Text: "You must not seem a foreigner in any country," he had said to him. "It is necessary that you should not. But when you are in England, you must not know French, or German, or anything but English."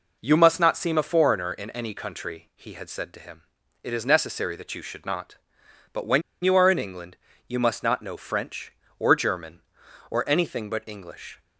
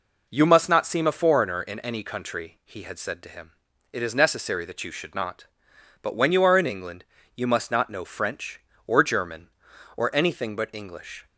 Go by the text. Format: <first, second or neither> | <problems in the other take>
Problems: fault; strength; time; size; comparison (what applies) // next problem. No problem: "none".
second | pauses between "when" and "you"; slight; at 6.2 s; 0.22 s long